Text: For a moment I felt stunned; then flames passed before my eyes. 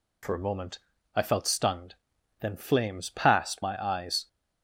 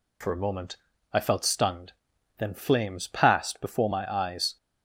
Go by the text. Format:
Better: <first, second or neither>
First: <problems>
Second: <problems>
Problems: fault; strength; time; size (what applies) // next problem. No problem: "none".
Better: second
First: pauses between "moment" and "I"; slight; at 0.7 s; 0.36 s long // skips "before"; at 3.6 s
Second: pauses between "moment" and "I"; slight; at 0.7 s; 0.36 s long